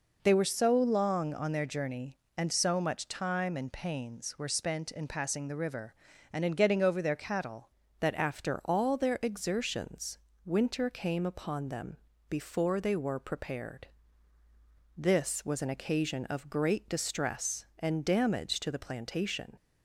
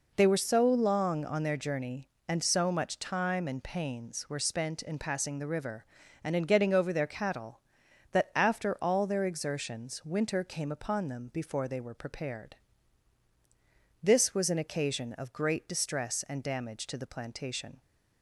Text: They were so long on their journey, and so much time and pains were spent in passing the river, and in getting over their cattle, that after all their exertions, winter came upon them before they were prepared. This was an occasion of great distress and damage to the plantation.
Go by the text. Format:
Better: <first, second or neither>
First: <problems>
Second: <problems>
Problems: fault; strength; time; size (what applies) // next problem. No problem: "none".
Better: second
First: changes voice at "that"; from 7.9 s on; 11.6 s long // pauses between "them" and "before"; slight; at 11.9 s; 0.32 s long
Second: none